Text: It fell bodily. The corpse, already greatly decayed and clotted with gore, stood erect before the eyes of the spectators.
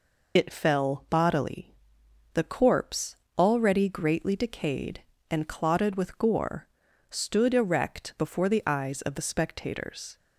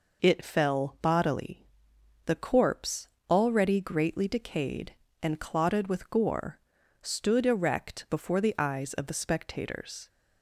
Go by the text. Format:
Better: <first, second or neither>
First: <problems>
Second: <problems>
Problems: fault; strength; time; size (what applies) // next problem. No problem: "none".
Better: second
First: loses the start of "It"; at 0.3 s; 55 ms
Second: none